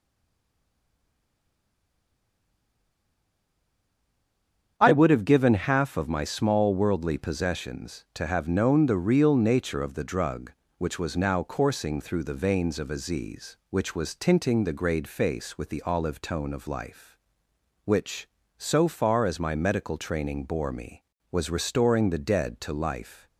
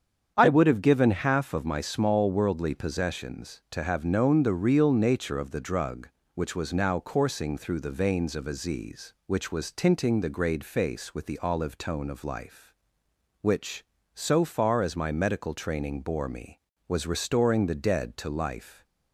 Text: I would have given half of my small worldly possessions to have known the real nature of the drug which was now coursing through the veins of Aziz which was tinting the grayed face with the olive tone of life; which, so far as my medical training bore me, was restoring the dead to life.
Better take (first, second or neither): second